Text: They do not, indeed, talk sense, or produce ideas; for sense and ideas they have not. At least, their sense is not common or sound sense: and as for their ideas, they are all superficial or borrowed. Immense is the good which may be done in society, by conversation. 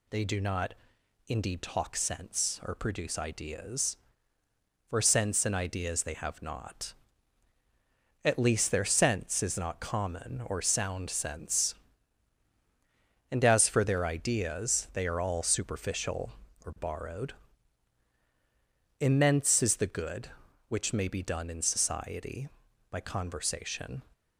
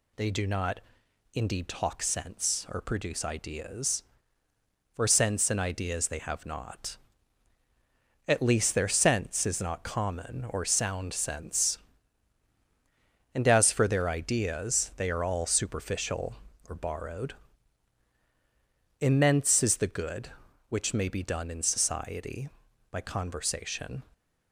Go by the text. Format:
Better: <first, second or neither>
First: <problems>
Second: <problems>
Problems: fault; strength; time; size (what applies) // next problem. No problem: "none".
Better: neither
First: none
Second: none